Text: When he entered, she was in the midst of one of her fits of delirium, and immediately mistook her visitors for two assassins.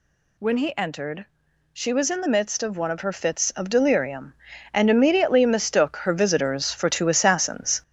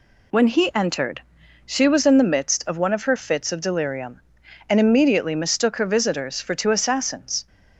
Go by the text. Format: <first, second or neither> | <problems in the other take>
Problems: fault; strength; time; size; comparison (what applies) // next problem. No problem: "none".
second | gets louder; noticeable; throughout; 5.5 dB